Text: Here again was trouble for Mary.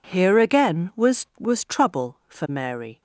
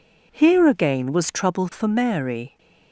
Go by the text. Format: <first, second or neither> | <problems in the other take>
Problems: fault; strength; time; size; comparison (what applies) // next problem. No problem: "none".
second | says "was" twice; at 1.3 s